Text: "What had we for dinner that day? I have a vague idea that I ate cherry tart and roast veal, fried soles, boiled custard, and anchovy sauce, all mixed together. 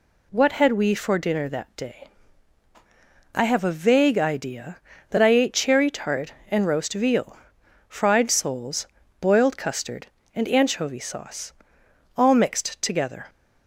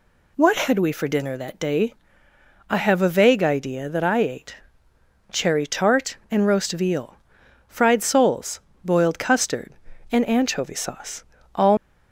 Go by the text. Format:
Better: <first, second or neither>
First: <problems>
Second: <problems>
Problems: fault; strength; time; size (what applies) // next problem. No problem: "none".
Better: first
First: none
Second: pauses between "ate" and "cherry"; noticeable; at 4.5 s; 0.76 s long // stops before "mixed together"; at 11.7 s